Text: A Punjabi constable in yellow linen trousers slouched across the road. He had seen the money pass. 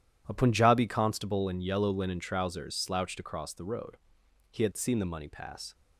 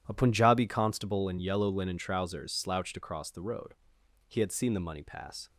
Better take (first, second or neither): neither